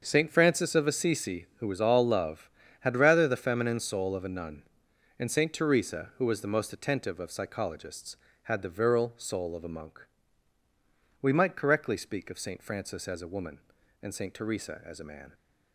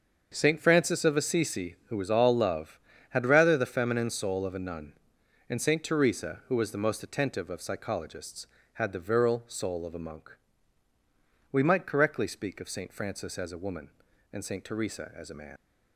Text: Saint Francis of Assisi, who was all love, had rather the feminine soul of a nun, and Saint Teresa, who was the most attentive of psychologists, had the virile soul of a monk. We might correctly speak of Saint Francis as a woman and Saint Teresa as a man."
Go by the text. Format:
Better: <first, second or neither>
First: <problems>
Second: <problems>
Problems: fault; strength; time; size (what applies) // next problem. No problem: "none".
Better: first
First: starts louder than the rest; until 1.0 s; 7 dB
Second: starts louder than the rest; until 1.3 s; 7 dB // leaves "man" unfinished; at 15.5 s; 85 ms